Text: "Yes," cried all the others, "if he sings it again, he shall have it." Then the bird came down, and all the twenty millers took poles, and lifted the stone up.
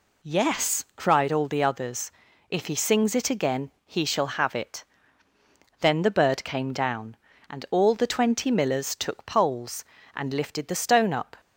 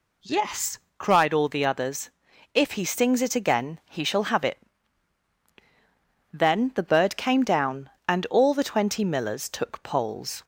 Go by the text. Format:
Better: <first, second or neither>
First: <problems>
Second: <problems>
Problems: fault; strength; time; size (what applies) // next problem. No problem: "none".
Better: first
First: none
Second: stops before "and lifted the stone up"; at 10.4 s